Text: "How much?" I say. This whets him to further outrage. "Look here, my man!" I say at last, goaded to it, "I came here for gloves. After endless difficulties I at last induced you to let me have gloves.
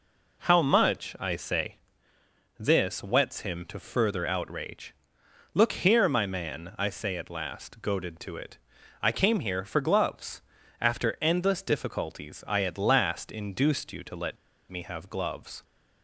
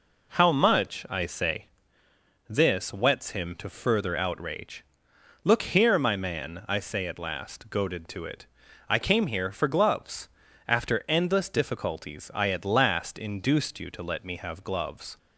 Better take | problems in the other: second | pauses between "let" and "me"; slight; at 14.3 s; 0.35 s long

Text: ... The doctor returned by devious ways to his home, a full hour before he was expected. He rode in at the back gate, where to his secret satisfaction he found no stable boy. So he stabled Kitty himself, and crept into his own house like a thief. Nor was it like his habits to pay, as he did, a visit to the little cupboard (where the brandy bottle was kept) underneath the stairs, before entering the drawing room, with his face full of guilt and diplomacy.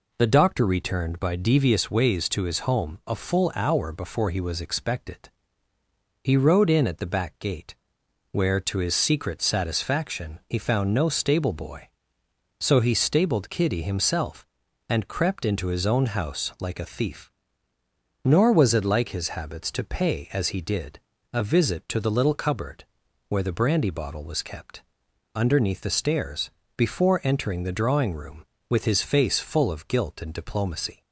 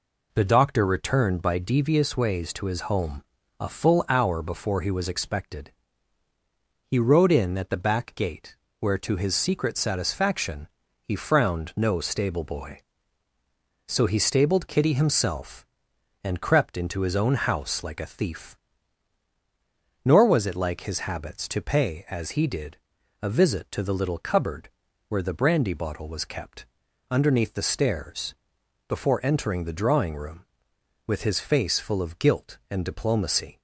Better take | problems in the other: first | pauses between "satisfaction" and "he"; slight; at 10.6 s; 0.34 s long // says "frowned" for "found"; at 11.1 s

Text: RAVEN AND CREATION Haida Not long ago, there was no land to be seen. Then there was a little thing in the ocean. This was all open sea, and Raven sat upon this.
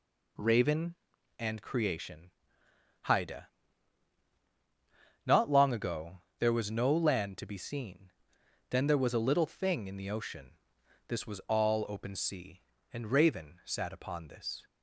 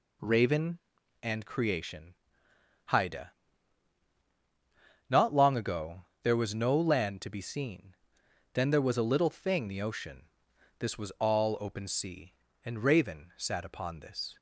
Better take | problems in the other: first | pauses between "CREATION" and "Haida"; noticeable; at 2.1 s; 0.76 s long; noticeable in the first // pauses between "Haida" and "Not"; strong; at 3.3 s; 1.7 s long; strong in the first // skips "in"; at 9.6 s

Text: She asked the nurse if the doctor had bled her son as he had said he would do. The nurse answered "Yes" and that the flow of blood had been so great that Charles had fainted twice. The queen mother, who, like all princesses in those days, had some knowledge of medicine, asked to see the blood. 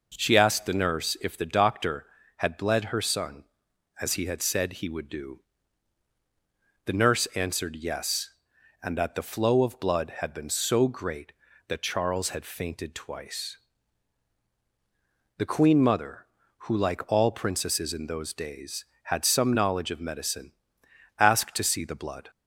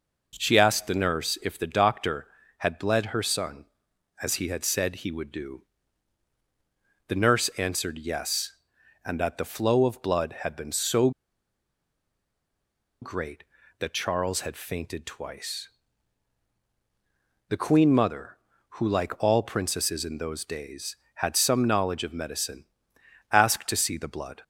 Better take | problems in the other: first | pauses between "so" and "great"; strong; at 11.0 s; 1.9 s long

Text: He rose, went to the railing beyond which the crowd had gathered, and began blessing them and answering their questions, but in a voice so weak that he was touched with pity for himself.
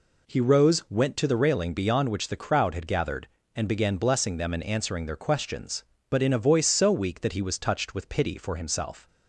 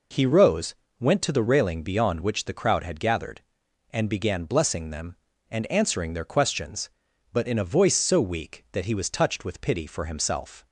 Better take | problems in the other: neither | none

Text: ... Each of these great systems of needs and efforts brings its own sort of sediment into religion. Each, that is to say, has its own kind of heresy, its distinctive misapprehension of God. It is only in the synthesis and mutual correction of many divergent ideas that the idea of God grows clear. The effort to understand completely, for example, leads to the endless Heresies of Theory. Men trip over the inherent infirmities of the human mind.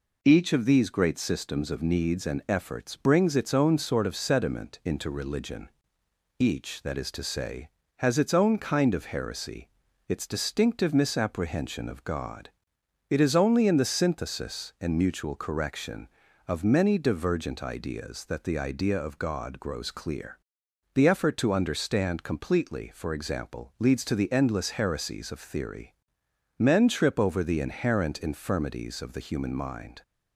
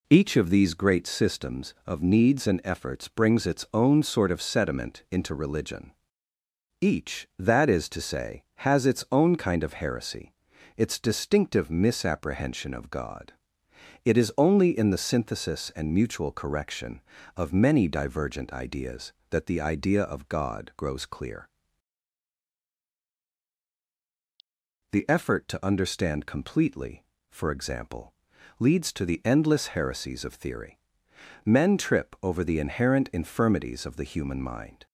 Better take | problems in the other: neither | none

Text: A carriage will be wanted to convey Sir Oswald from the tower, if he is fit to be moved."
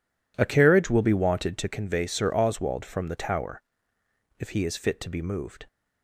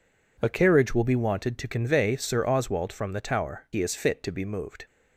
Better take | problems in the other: first | skips "if"; at 3.6 s

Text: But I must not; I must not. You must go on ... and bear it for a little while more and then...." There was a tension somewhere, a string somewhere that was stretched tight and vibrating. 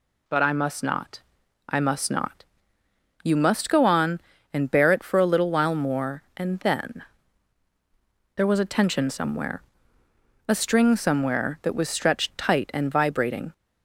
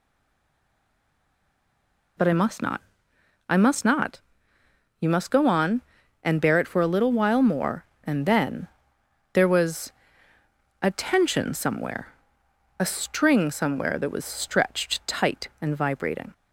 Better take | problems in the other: first | stays silent before the first word; until 2.1 s; 2.1 s long // pauses between "was" and "a"; noticeable; at 9.9 s; 0.88 s long

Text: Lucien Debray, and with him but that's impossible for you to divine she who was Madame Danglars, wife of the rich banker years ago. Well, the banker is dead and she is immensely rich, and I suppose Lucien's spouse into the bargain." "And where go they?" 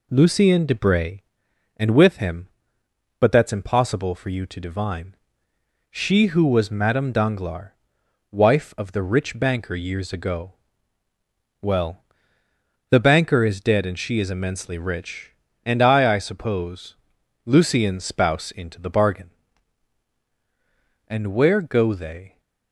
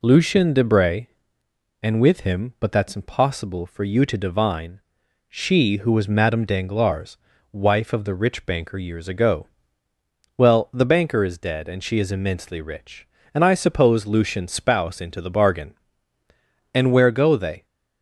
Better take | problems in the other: second | pauses between "divine" and "she"; noticeable; at 5.1 s; 0.78 s long; noticeable in the second // says "I" twice; at 16.1 s // pauses between "suppose" and "Lucien's"; noticeable; at 16.9 s; 0.50 s long

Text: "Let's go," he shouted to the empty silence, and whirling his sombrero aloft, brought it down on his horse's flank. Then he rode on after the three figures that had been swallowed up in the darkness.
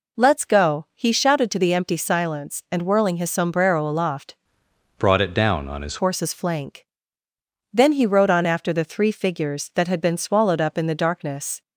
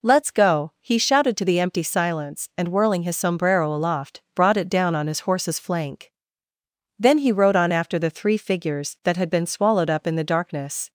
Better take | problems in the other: second | changes voice from "brought" to "his"; from 4.9 to 5.9 s; 1.0 s long

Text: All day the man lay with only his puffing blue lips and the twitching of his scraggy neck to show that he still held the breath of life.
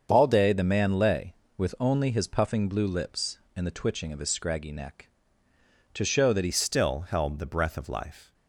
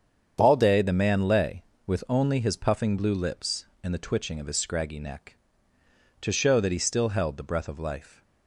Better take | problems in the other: second | starts louder than the rest; until 1.1 s; 7 dB; strong in the second // changes voice at "still"; from 6.5 s on; 1.8 s long

